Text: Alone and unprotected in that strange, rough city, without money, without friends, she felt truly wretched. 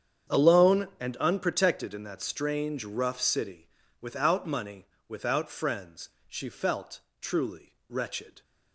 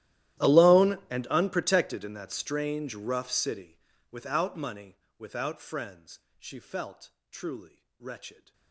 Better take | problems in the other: first | gets quieter; strong; throughout; 25.5 dB // starts louder than the rest; strong; until 1.5 s; 13.5 dB; strong in the first // pauses between "felt" and "truly"; slight; at 7.1 s; 0.22 s long; slight in the first // pauses between "truly" and "wretched"; slight; at 7.8 s; 0.16 s long; slight in the first

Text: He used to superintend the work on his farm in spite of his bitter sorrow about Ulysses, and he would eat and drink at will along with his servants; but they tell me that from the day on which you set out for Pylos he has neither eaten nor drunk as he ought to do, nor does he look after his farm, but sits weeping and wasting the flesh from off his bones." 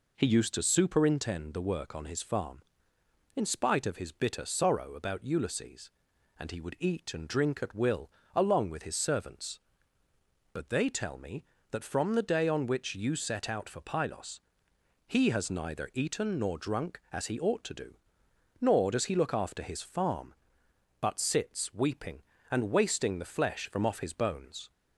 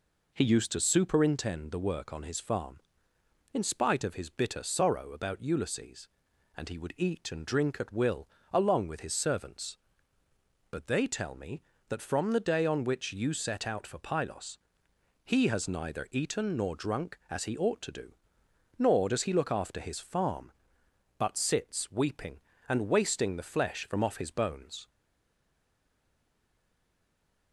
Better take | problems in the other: first | pauses between "will" and "along"; slight; at 8.2 s; 0.24 s long; slight in the first // pauses between "Pylos" and "he"; noticeable; at 14.5 s; 0.66 s long; noticeable in the first // stays silent after the last word; strong; from 24.8 s on; 2.7 s long

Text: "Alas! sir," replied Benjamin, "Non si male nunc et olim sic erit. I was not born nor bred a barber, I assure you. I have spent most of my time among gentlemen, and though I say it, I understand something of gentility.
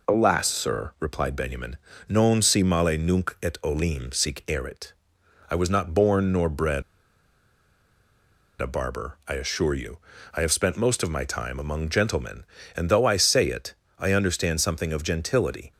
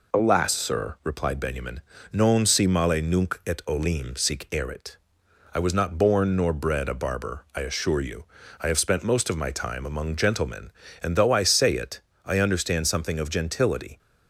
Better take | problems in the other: second | pauses between "bred" and "a"; strong; at 6.8 s; 1.7 s long

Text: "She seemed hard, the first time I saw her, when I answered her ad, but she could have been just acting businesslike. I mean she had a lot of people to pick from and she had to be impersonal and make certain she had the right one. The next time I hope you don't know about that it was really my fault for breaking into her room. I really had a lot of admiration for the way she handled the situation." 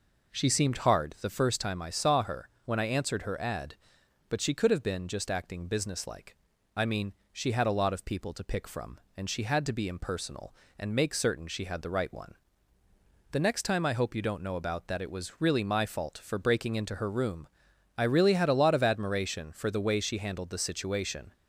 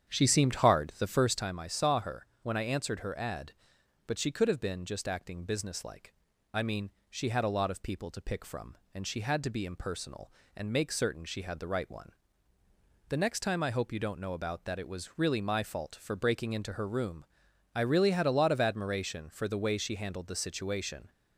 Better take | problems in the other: first | starts louder than the rest; strong; until 1.5 s; 8.5 dB // pauses between "mean" and "she"; slight; at 6.9 s; 0.20 s long; slight in the first

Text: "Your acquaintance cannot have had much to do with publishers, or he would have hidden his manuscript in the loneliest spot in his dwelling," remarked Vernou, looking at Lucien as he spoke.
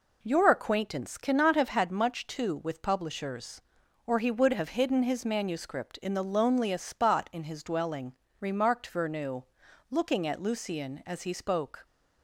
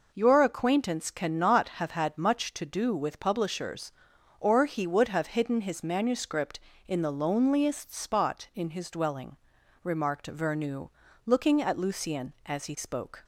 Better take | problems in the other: second | skips "do"; at 2.5 s

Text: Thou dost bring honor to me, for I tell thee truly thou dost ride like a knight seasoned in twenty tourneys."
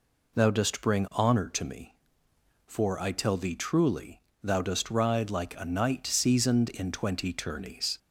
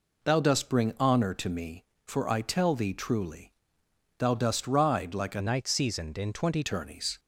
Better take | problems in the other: first | pauses between "truly" and "thou"; noticeable; at 3.4 s; 0.70 s long; slight in the first // changes voice from "knight" to "twenty"; from 5.3 to 6.6 s; 1.3 s long

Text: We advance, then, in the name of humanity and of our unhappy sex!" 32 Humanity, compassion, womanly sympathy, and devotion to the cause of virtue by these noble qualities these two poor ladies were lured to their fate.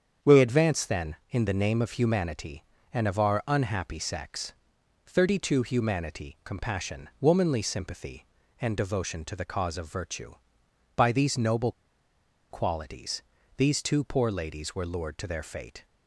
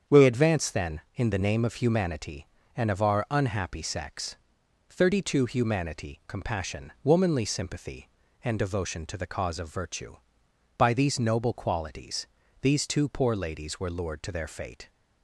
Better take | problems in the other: second | starts louder than the rest; strong; until 1.3 s; 7.5 dB; strong in the second // pauses between "noble" and "qualities"; noticeable; at 11.7 s; 0.78 s long // pauses between "qualities" and "these"; slight; at 13.2 s; 0.32 s long; slight in the second

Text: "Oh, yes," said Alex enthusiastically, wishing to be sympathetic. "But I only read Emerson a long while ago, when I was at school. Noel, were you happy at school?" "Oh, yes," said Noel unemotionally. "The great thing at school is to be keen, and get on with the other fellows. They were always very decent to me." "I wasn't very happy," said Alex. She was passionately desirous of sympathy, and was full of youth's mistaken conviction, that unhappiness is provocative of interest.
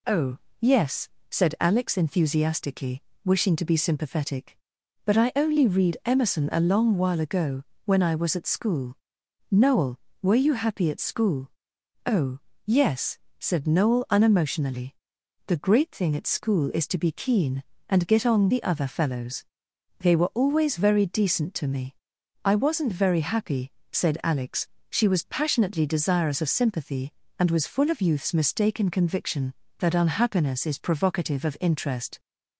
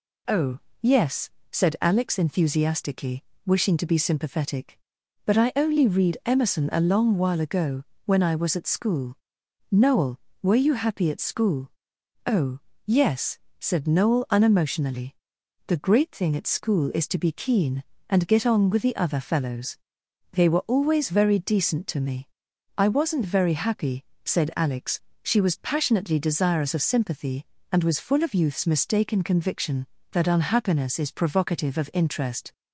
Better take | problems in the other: second | skips "with"; at 18.5 s

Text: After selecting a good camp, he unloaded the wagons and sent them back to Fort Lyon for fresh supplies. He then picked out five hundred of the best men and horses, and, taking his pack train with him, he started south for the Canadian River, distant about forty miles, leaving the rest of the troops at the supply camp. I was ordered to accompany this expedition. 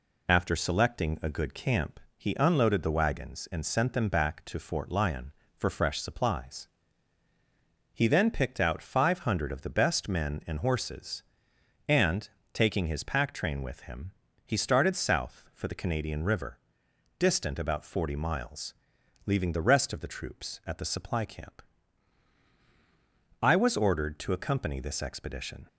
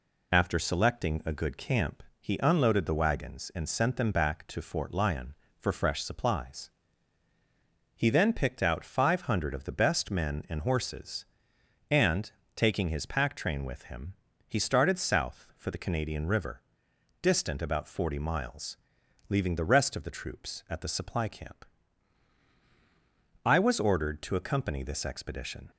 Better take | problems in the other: neither | none

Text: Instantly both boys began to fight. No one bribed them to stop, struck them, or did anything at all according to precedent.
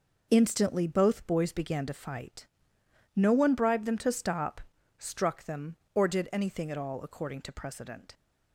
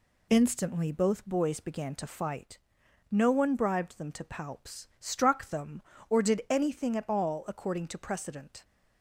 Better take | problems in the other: first | says "palps" for "stop"; at 4.2 s

